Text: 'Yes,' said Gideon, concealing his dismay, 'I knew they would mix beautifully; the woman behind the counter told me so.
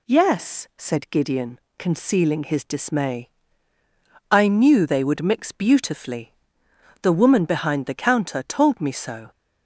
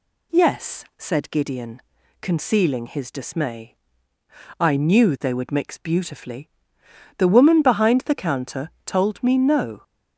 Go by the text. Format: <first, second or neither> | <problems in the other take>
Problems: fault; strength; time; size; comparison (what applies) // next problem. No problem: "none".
first | pauses between "counter" and "told"; slight; at 8.7 s; 0.16 s long // says "no" for "so"; at 9.3 s